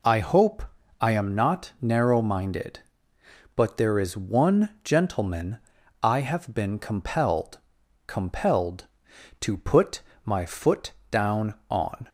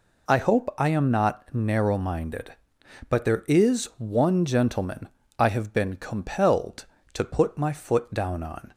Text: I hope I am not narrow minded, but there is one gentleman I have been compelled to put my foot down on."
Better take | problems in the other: second | pauses between "hope" and "I"; slight; at 0.6 s; 0.36 s long // pauses between "gentleman" and "I"; at 5.5 s; 0.44 s long; slight in the second // says "compelled" twice; at 8.0 s // pauses between "put" and "my"; slight; at 10.0 s; 0.24 s long // pauses between "foot" and "down"; slight; at 10.9 s; 0.20 s long

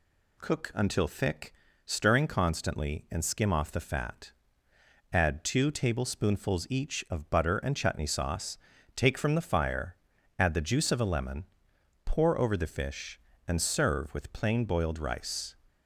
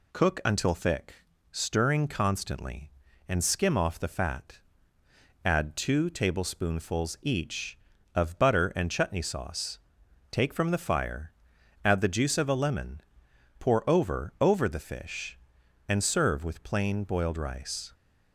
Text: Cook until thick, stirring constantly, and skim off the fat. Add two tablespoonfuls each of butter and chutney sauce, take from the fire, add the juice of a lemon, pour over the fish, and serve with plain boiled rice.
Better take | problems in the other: first | says "over" twice; at 14.4 s

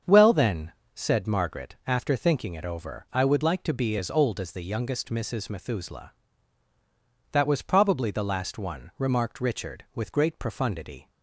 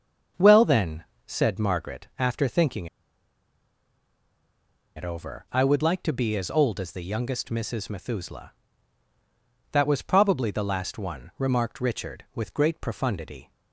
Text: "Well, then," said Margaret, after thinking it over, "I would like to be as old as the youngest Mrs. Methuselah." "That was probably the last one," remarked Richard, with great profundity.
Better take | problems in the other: first | starts louder than the rest; until 1.5 s; 7 dB; also in the first // pauses between "thinking" and "it"; strong; at 2.8 s; 2.0 s long

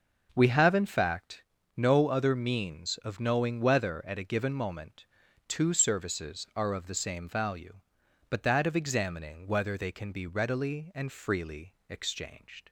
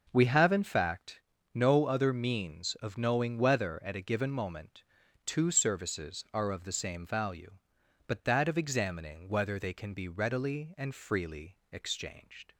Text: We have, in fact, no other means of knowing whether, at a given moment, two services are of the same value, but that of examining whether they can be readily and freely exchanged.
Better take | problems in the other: neither | pauses between "freely" and "exchanged"; slight; the same in both

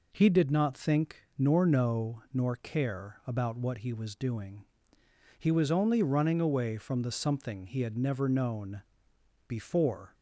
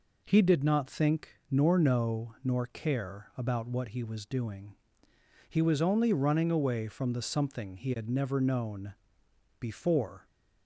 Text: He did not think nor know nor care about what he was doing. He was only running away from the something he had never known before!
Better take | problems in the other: neither | pauses between "known" and "before"; noticeable; the same in both

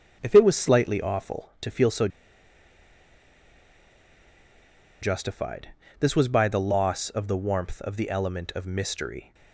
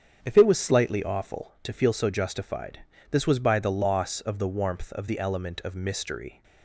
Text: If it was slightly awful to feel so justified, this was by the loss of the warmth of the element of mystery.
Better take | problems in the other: second | starts louder than the rest; strong; until 1.2 s; 8 dB; strong in the second // pauses between "so" and "justified"; strong; at 2.0 s; 2.9 s long

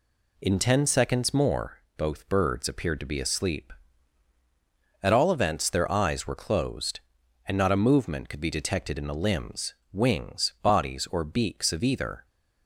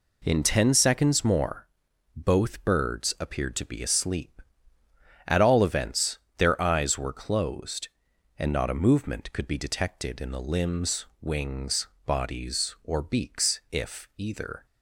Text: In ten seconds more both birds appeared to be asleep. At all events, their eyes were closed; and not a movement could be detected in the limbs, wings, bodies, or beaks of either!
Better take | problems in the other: first | pauses between "more" and "both"; noticeable; at 1.6 s; 0.48 s long; slight in the first // says "if" for "of"; at 13.7 s

